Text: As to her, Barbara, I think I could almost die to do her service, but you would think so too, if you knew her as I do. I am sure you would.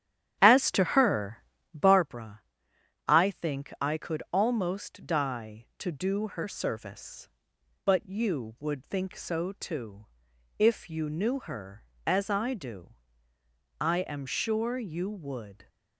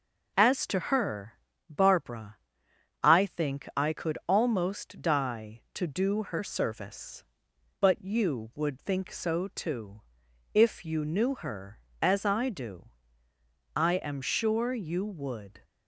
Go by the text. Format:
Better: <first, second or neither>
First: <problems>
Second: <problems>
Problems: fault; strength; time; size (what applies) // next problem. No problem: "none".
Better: second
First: starts louder than the rest; strong; until 2.1 s; 10 dB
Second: none